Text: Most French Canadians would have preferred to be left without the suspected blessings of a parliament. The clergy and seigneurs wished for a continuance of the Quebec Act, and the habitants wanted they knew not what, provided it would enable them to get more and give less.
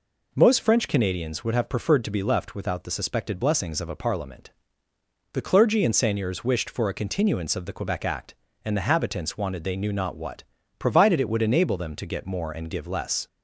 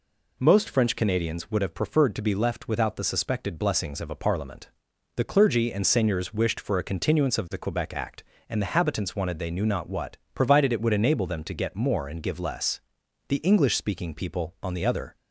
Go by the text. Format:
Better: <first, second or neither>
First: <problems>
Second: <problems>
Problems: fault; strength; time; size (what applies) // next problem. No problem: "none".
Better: first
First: none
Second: goes on to say "The English speaking people on the other"; strong; from 13.2 s on; 1.9 s long